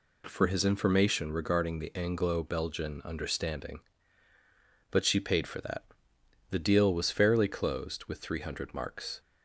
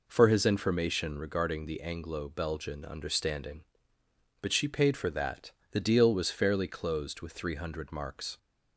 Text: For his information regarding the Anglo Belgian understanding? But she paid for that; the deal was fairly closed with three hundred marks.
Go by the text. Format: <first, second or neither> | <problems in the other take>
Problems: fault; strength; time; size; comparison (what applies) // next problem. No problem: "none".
neither | none